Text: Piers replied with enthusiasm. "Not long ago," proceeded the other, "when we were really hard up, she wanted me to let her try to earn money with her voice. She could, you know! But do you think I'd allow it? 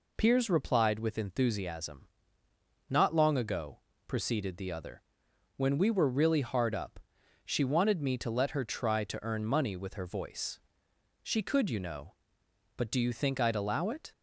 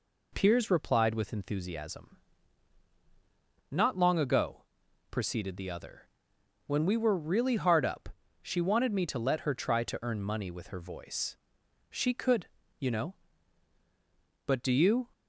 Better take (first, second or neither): first